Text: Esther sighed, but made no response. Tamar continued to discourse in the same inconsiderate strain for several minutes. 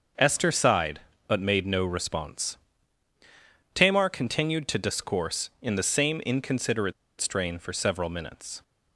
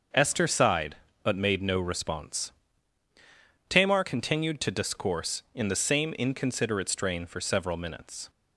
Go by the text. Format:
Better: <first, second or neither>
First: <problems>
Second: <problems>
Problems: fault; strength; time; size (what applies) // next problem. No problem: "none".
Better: second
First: starts louder than the rest; until 1.4 s; 6.5 dB // pauses between "inconsiderate" and "strain"; slight; at 6.9 s; 0.27 s long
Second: starts louder than the rest; until 1.3 s; 6.5 dB